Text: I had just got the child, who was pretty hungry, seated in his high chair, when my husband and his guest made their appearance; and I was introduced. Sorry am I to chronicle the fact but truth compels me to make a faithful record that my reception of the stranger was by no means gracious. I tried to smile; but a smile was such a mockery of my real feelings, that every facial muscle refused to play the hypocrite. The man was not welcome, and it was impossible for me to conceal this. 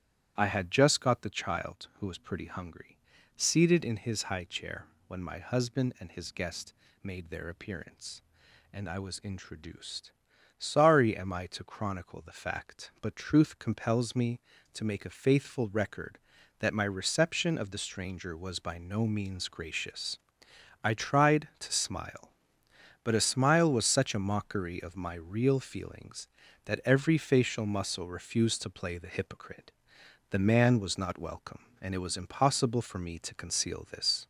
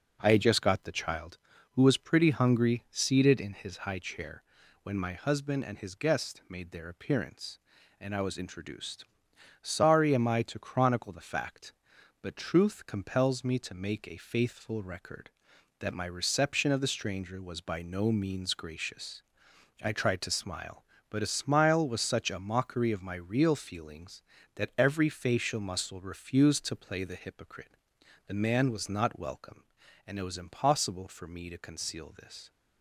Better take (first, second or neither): second